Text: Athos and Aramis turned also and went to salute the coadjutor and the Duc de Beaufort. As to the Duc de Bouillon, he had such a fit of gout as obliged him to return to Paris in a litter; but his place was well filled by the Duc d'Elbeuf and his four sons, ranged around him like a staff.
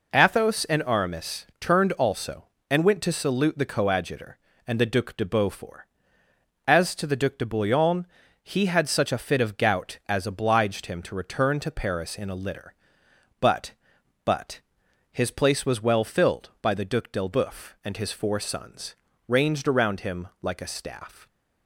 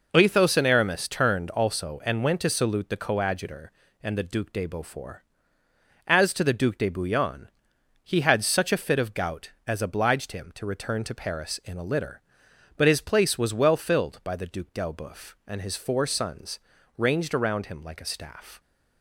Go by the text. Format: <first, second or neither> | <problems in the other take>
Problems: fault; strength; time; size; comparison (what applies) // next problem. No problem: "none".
second | says "but" twice; at 14.2 s